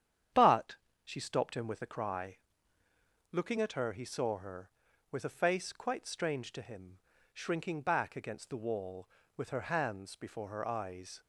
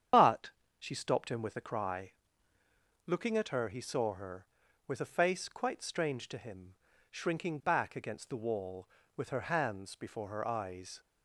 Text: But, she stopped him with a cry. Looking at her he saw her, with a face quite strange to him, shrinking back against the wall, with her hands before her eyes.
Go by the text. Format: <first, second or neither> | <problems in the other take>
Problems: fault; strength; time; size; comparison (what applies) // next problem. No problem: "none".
first | loses the start of "But"; at 0.1 s; 55 ms // starts louder than the rest; strong; until 1.4 s; 8.5 dB; strong in the first